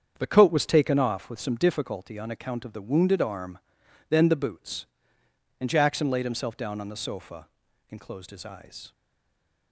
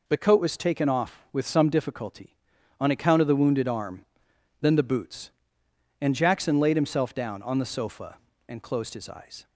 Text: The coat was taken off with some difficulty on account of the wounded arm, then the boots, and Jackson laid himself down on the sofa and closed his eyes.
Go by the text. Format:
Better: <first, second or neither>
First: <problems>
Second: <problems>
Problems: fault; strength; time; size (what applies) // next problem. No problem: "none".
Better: second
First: starts louder than the rest; strong; until 1.1 s; 7.5 dB // stays silent after the last word; slight; from 8.9 s on; 0.8 s long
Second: none